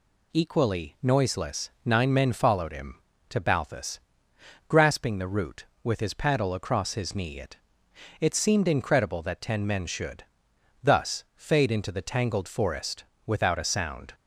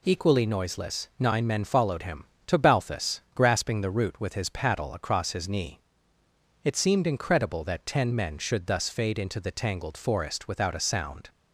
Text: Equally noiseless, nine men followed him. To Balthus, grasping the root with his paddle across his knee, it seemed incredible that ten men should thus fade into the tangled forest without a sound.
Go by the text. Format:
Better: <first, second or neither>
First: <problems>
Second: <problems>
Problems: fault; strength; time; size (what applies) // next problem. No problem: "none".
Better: second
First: says "it" twice; at 8.2 s // pauses between "should" and "thus"; noticeable; at 10.2 s; 0.62 s long // pauses between "forest" and "without"; slight; at 13.0 s; 0.24 s long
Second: none